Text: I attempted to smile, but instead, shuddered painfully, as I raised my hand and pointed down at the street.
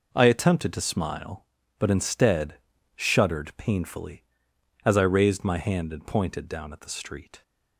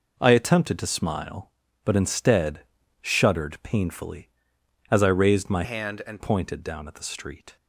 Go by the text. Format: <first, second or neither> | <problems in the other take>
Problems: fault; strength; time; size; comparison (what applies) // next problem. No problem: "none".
first | changes voice from "hand" to "and"; from 5.6 to 6.1 s; 0.5 s long